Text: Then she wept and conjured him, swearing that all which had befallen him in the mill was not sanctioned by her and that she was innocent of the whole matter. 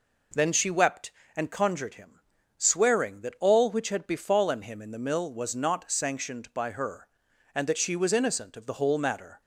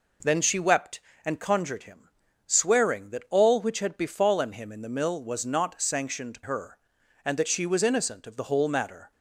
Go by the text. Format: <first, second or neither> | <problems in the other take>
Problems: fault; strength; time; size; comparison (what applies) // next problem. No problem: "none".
first | skips "by"; at 6.4 s